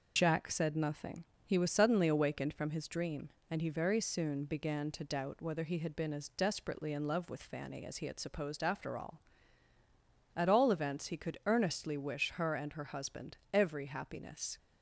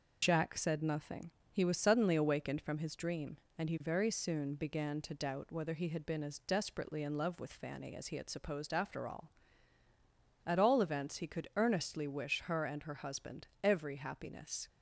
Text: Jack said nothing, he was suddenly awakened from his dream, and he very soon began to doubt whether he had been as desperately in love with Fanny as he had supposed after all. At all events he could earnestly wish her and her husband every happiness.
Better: neither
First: pauses between "husband" and "every"; slight; at 13.3 s; 0.16 s long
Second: pauses between "husband" and "every"; slight; at 13.4 s; 0.16 s long

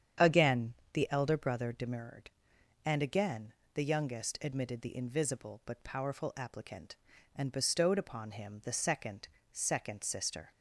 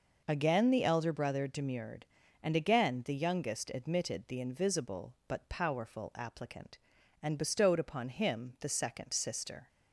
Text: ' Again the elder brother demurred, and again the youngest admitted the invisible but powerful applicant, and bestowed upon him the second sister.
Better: second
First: starts louder than the rest; strong; until 1.4 s; 8.5 dB // pauses between "Again" and "the"; slight; at 0.7 s; 0.22 s long // pauses between "again" and "the"; slight; at 3.5 s; 0.22 s long // says "second" twice; at 9.5 s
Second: none

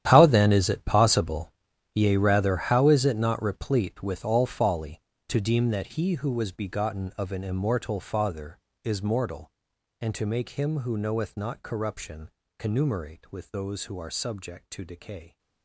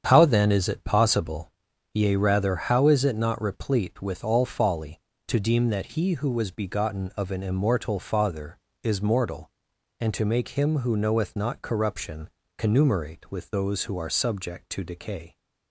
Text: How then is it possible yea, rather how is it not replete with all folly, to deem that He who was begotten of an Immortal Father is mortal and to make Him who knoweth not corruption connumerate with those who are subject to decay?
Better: second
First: gets quieter; strong; throughout; 16.5 dB // starts louder than the rest; strong; until 1.1 s; 11 dB // pauses between "possible" and "yea"; at 1.5 s; 0.40 s long // pauses between "corruption" and "connumerate"; slight; at 12.3 s; 0.30 s long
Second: starts louder than the rest; strong; until 1.1 s; 8 dB // pauses between "possible" and "yea"; at 1.5 s; 0.40 s long // pauses between "corruption" and "connumerate"; slight; at 12.2 s; 0.30 s long

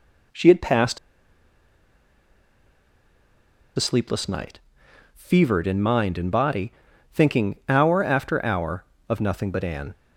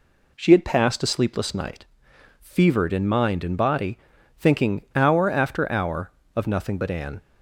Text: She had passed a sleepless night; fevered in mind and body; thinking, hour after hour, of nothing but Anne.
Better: second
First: pauses between "passed" and "a"; strong; at 0.9 s; 2.7 s long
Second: none

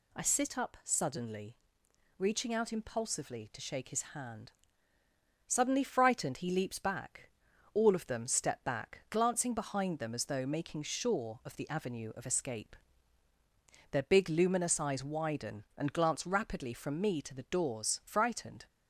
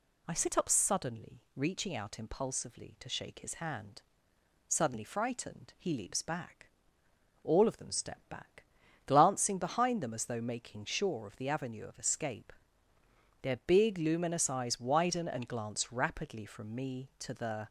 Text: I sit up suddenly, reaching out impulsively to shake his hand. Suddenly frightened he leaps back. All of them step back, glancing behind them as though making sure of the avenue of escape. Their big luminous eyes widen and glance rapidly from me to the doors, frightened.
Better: first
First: none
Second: stops before "doors frightened"; at 17.6 s

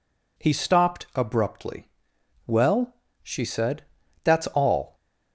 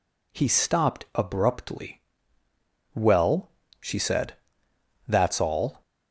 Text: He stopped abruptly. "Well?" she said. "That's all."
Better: neither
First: none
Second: none

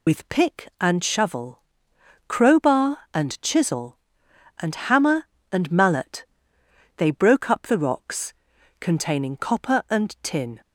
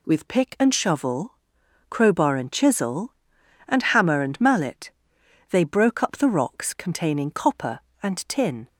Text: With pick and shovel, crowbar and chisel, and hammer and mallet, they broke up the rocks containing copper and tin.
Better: second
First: loses the start of "With"; at 0.0 s; 45 ms // pauses between "rocks" and "containing"; at 8.3 s; 0.44 s long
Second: none

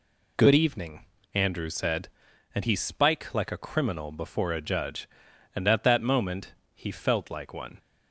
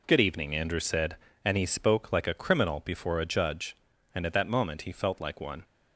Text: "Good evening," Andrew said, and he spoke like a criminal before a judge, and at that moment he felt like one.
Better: second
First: says "spike" for "spoke"; at 2.7 s // pauses between "moment" and "he"; slight; at 6.5 s; 0.22 s long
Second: none

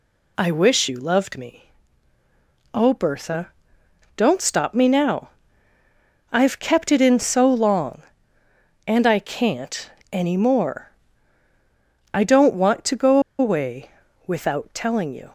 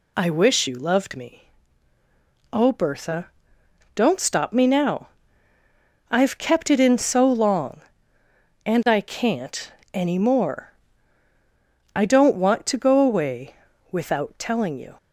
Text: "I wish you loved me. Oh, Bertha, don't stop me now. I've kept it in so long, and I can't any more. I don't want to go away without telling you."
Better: second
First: pauses between "can't" and "any"; slight; at 9.8 s; 0.22 s long // pauses between "go" and "away"; slight; at 13.1 s; 0.21 s long // pauses between "away" and "without"; slight; at 13.9 s; 0.34 s long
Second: pauses between "can't" and "any"; slight; at 9.7 s; 0.22 s long // pauses between "away" and "without"; slight; at 13.5 s; 0.34 s long

